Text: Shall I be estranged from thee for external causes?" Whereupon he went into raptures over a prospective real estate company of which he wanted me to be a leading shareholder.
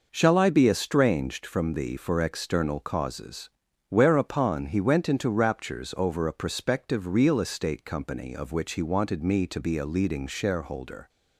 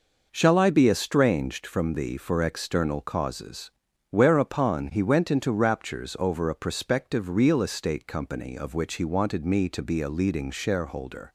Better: neither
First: none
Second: none

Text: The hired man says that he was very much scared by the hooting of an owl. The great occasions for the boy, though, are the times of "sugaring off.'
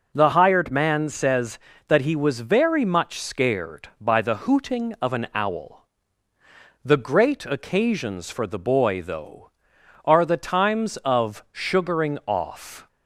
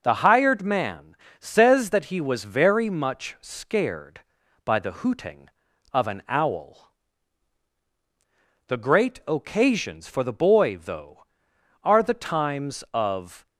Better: first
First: none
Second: pauses between "man" and "says"; slight; at 1.1 s; 0.24 s long // stops before "sugaring off"; at 13.4 s

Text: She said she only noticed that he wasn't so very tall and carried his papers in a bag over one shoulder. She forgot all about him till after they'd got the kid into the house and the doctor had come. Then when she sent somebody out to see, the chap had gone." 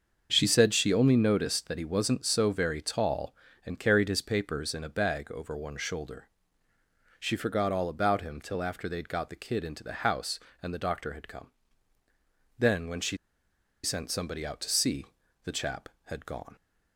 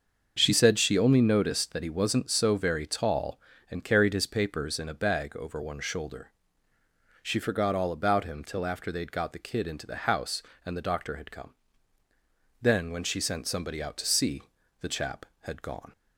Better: second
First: starts louder than the rest; until 1.3 s; 6.5 dB // pauses between "she" and "sent"; noticeable; at 13.1 s; 0.66 s long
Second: starts louder than the rest; until 1.3 s; 6.5 dB

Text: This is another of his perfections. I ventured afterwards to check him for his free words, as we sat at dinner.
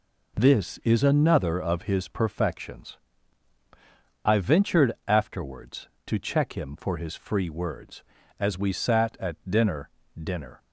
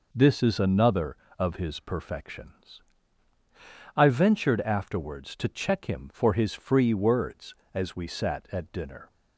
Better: second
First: pauses between "ventured" and "afterwards"; slight; at 4.9 s; 0.16 s long // says "dinner" twice; at 10.2 s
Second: none

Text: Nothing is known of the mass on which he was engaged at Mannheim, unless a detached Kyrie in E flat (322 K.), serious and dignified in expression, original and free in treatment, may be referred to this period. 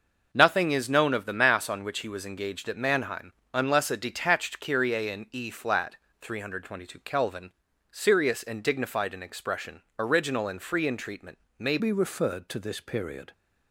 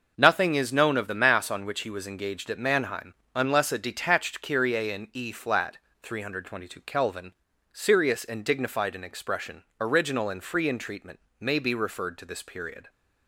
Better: second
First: changes voice at "be"; from 11.7 s on; 1.6 s long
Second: none

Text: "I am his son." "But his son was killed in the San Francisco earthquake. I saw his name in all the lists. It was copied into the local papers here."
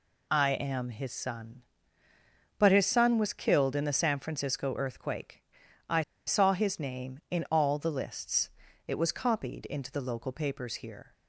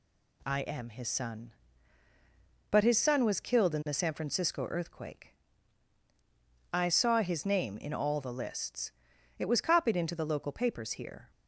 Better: second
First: pauses between "I" and "saw"; slight; at 6.0 s; 0.25 s long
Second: none

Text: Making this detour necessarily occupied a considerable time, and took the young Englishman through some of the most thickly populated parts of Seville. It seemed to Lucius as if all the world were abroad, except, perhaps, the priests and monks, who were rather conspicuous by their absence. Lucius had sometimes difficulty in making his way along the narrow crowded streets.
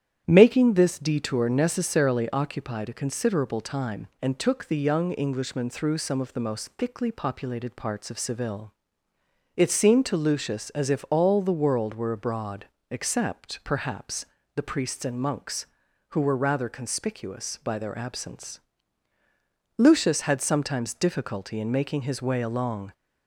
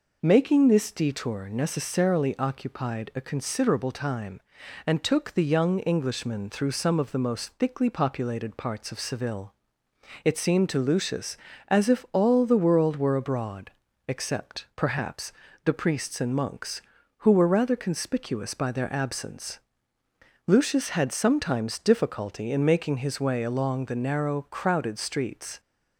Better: second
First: starts louder than the rest; strong; until 1.2 s; 10 dB // stops before "the narrow crowded streets"; at 22.9 s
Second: none

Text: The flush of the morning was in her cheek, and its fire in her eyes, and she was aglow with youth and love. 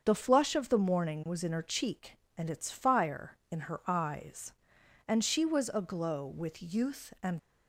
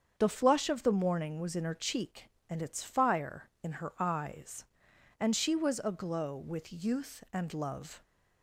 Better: second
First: starts louder than the rest; until 1.0 s; 7 dB // stops before "love"; at 7.3 s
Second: starts louder than the rest; strong; until 1.2 s; 7.5 dB

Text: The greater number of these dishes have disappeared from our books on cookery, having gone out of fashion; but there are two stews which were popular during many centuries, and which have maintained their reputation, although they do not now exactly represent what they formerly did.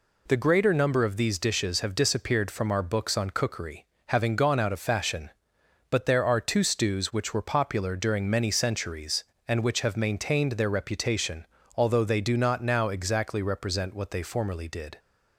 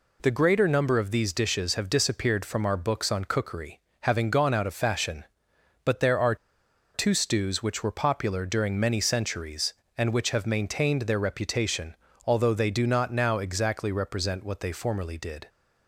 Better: first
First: none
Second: pauses between "are" and "two"; noticeable; at 6.3 s; 0.59 s long

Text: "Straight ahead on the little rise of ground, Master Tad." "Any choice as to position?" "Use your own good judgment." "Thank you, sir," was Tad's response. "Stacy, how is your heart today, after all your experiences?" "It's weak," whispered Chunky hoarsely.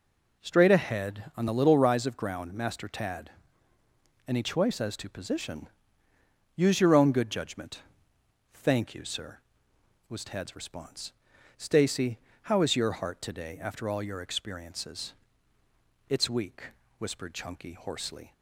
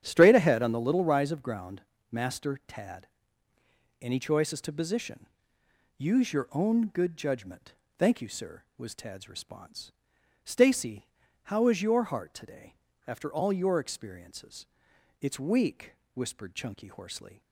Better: first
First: none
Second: starts louder than the rest; strong; until 1.2 s; 9.5 dB

